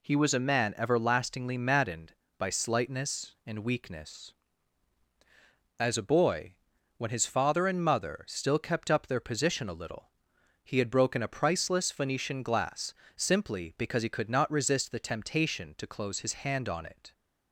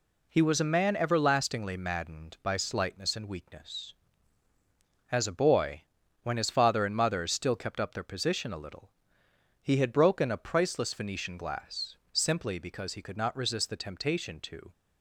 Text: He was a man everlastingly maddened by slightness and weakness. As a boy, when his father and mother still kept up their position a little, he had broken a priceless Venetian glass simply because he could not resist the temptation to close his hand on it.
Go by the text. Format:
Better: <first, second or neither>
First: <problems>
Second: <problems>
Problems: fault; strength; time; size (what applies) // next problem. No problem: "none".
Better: first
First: pauses between "glass" and "simply"; slight; at 12.9 s; 0.22 s long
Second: pauses between "glass" and "simply"; slight; at 11.9 s; 0.18 s long // stops before "close his hand on it"; at 14.7 s